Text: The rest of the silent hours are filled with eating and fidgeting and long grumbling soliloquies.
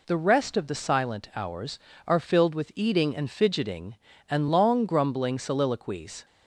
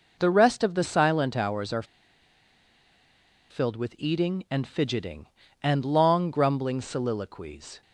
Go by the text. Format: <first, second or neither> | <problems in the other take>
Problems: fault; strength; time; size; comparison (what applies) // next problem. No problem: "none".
first | pauses between "are" and "filled"; strong; at 1.8 s; 1.6 s long